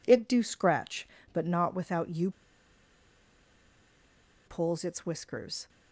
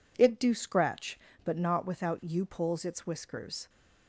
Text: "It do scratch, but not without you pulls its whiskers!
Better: second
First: pauses between "you" and "pulls"; strong; at 2.3 s; 2.1 s long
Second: none

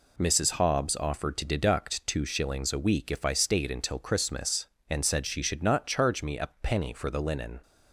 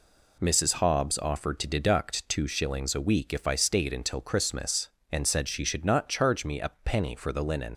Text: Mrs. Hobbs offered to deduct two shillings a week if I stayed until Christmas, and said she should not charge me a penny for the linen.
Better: first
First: none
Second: leaves "linen" unfinished; at 7.7 s; 90 ms

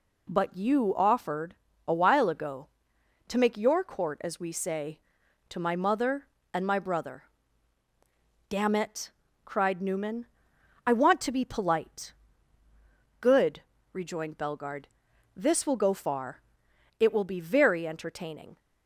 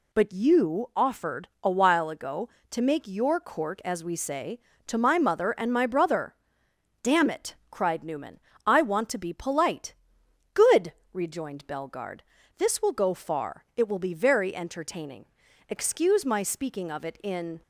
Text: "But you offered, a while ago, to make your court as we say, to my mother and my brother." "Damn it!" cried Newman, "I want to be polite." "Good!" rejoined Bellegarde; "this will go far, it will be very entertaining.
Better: first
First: none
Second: goes on to say "Excuse my speaking of it in"; strong; from 15.6 s on; 1.9 s long

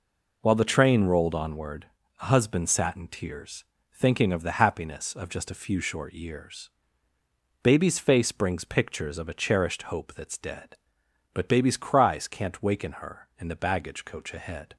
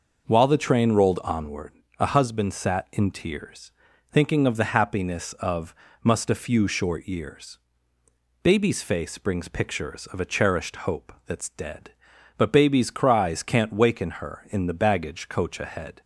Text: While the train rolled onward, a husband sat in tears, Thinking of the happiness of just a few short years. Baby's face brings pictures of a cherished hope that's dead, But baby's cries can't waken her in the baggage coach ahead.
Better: first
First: none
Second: says "must" for "just"; at 6.0 s

